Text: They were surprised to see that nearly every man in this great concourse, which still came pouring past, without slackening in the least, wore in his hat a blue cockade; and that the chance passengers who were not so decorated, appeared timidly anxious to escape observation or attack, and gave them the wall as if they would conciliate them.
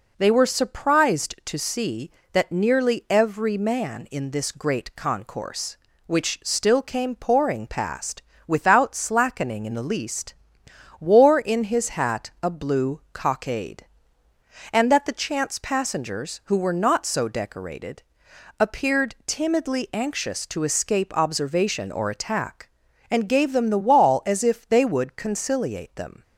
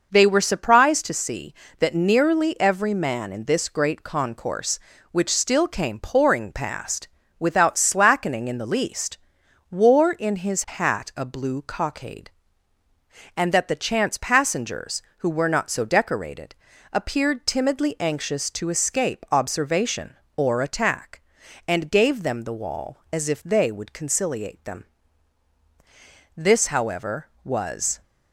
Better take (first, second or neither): first